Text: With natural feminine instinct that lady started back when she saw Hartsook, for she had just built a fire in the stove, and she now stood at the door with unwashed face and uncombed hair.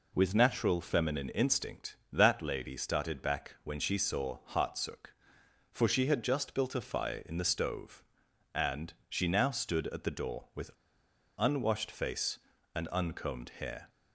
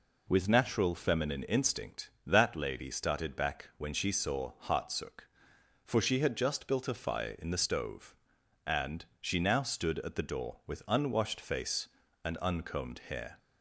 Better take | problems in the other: second | pauses between "and" and "she"; slight; at 8.9 s; 0.16 s long; slight in the second // pauses between "with" and "unwashed"; noticeable; at 10.7 s; 0.68 s long

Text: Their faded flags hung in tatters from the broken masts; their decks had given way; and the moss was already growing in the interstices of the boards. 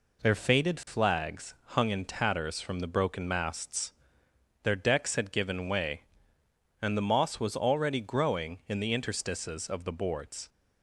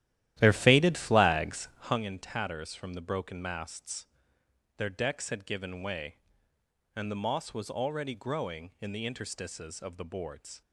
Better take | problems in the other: first | starts louder than the rest; strong; until 2.0 s; 13 dB

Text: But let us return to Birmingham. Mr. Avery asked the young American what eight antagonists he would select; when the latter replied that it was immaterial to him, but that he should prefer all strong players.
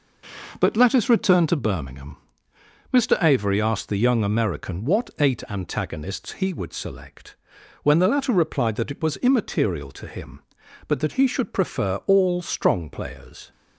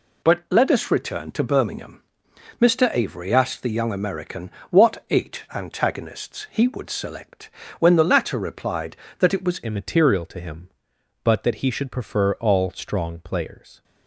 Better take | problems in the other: first | pauses between "American" and "what"; slight; at 4.5 s; 0.20 s long // changes voice at "immaterial"; from 9.6 s on; 4.2 s long

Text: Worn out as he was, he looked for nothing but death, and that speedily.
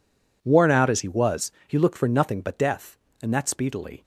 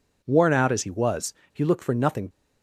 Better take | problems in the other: first | stops before "but death and that speedily"; at 2.3 s

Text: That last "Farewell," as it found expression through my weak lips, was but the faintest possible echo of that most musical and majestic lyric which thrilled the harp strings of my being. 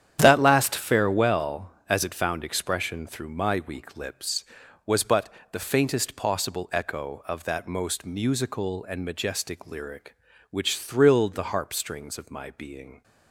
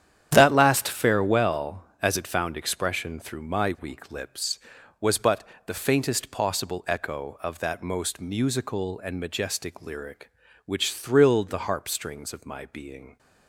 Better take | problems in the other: neither | starts louder than the rest; strong; the same in both // pauses between "but" and "the"; slight; the same in both

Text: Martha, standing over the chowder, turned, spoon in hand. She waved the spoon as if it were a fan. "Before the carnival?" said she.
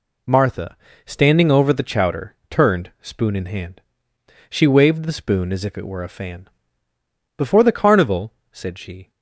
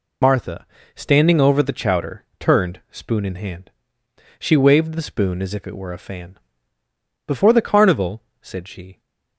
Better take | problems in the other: first | loses the start of "Martha"; at 0.2 s; 65 ms

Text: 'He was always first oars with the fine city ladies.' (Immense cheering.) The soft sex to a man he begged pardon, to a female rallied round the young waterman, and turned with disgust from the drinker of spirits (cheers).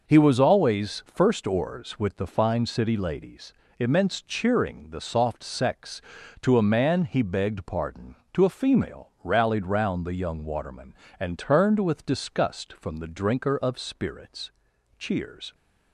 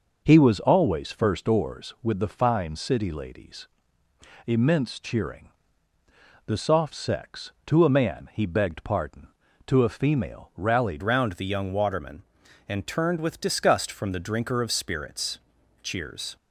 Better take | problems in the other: first | changes voice at "round"; from 11.0 s on; 5.3 s long

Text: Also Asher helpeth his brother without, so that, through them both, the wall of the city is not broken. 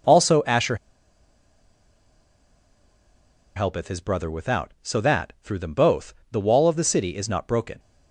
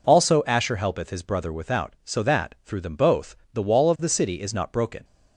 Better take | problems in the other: second | pauses between "Asher" and "helpeth"; strong; at 0.7 s; 2.8 s long

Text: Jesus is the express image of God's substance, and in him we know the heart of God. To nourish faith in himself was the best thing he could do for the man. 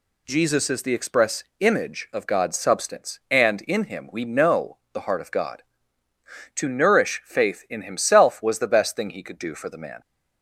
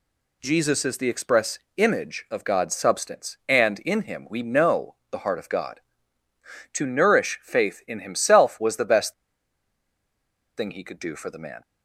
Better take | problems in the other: first | pauses between "express" and "image"; slight; at 1.5 s; 0.18 s long; slight in the first // pauses between "know" and "the"; slight; at 4.9 s; 0.16 s long; slight in the first // pauses between "best" and "thing"; strong; at 9.1 s; 1.4 s long

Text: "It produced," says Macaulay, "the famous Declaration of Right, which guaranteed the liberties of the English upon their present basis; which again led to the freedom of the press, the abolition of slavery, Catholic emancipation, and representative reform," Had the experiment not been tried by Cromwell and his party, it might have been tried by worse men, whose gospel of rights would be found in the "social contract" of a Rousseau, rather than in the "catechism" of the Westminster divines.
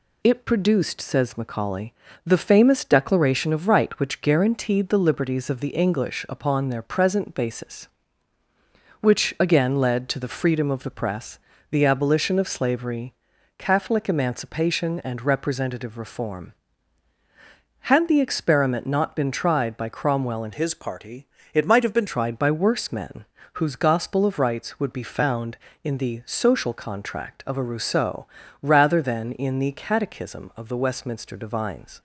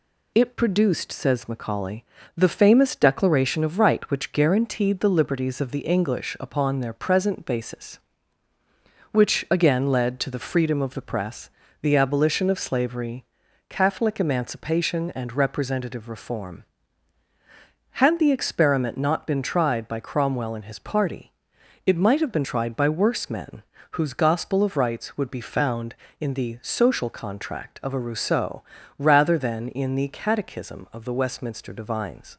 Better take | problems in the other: second | changes voice from "his" to "been"; from 20.5 to 22.0 s; 1.5 s long

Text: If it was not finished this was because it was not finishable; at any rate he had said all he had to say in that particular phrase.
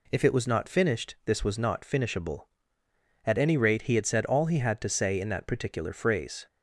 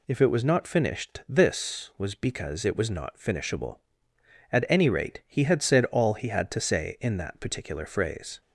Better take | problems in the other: second | skips "was because it"; at 1.4 s

